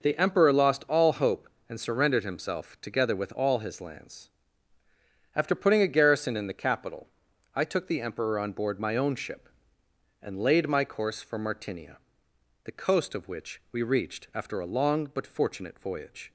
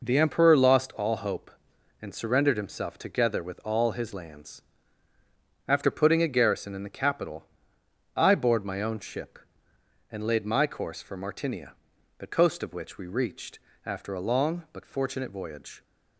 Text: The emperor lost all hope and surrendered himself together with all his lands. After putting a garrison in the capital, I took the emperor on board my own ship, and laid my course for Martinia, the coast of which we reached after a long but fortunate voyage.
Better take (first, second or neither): first